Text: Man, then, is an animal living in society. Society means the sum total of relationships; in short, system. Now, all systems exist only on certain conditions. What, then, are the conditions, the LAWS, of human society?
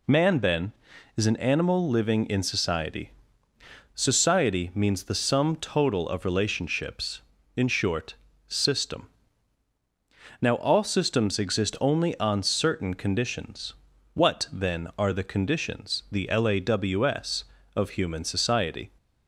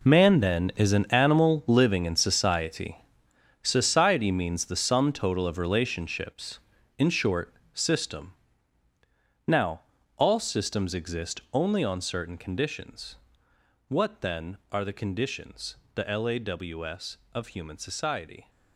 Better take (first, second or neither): first